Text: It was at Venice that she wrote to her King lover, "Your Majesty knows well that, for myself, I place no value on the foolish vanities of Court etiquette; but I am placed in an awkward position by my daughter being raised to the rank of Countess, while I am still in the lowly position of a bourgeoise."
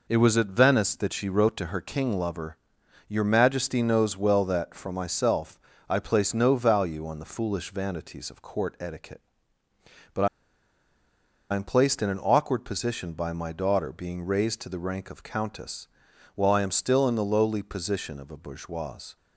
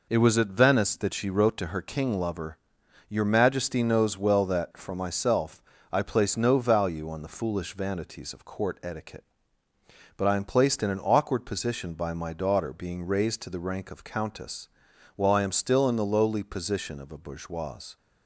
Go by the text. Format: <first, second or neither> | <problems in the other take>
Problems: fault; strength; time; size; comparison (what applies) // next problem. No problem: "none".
second | pauses between "but" and "I"; strong; at 10.2 s; 1.2 s long